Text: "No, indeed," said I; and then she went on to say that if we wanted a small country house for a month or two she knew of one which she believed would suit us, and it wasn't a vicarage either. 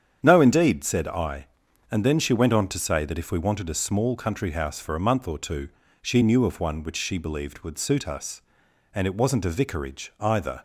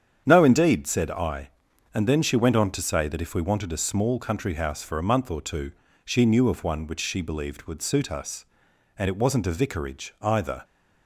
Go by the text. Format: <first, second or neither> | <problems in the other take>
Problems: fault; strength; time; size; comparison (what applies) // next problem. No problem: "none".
neither | starts louder than the rest; strong; the same in both // pauses between "two" and "she"; slight; the same in both